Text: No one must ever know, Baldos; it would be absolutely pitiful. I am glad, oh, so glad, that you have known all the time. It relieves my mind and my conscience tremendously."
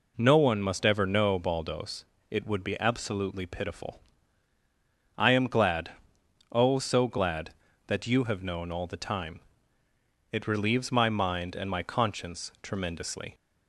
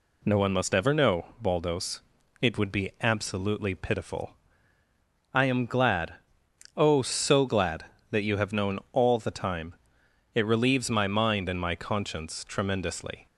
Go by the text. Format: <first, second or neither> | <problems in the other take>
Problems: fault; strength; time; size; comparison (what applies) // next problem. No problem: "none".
neither | none